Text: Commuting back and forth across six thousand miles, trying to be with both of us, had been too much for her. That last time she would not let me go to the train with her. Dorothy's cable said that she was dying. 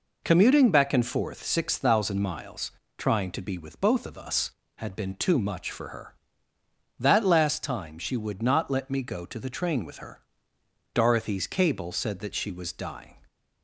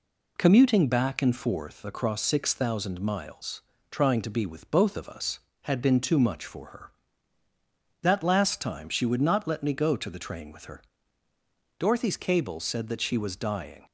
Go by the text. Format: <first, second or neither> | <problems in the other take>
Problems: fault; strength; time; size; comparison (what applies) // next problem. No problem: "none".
second | skips "across"; at 1.4 s